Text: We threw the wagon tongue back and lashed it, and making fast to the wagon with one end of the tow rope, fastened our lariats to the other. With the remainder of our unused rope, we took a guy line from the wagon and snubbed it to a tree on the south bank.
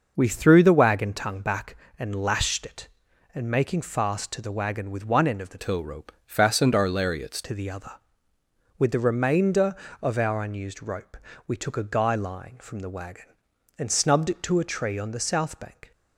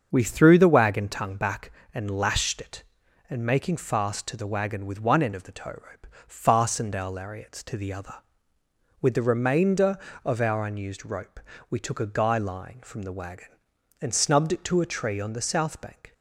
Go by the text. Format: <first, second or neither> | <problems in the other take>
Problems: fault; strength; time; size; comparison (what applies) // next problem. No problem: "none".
second | starts louder than the rest; noticeable; until 1.1 s; 6 dB; also in the second // changes voice from "tow" to "lariats"; from 5.5 to 7.3 s; 1.8 s long